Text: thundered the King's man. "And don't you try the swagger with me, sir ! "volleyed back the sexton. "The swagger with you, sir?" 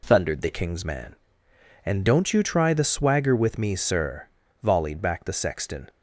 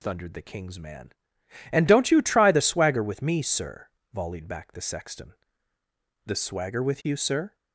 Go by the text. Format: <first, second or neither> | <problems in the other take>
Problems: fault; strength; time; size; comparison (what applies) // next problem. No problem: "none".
second | stops before "The swagger with you sir"; at 5.8 s